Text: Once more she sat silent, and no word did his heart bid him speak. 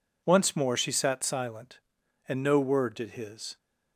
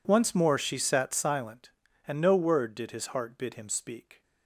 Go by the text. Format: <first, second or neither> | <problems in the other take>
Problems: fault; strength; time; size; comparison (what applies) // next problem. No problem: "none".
second | stops before "heart bid him speak"; at 3.5 s